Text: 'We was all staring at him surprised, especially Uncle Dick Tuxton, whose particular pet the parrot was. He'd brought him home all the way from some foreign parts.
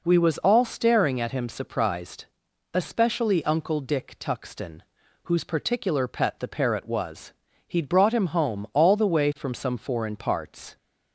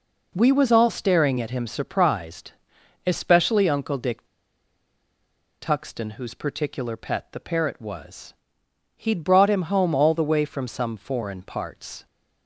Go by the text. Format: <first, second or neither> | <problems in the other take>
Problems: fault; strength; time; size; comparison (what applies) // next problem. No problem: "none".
first | pauses between "Dick" and "Tuxton"; strong; at 4.2 s; 1.3 s long